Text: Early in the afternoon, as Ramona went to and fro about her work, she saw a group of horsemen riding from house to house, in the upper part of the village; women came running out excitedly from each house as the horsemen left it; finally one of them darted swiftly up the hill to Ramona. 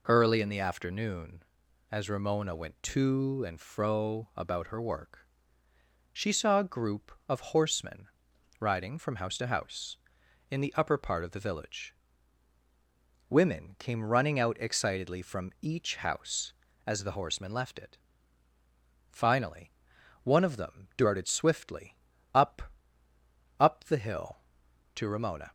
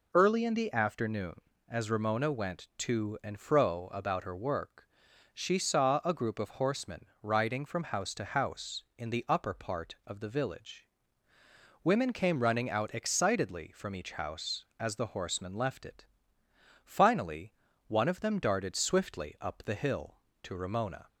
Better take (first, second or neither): second